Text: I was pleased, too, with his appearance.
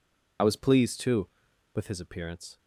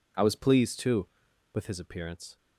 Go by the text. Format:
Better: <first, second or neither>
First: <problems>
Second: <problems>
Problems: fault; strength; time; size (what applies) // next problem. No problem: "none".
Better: second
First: loses the start of "I"; at 0.3 s; 25 ms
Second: none